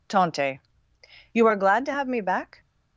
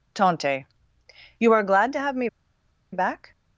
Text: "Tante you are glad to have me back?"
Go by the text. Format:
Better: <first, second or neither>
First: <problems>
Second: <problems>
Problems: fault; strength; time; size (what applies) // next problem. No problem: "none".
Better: first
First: pauses between "Tante" and "you"; noticeable; at 0.6 s; 0.72 s long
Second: pauses between "Tante" and "you"; noticeable; at 0.6 s; 0.72 s long // pauses between "me" and "back"; noticeable; at 2.2 s; 0.64 s long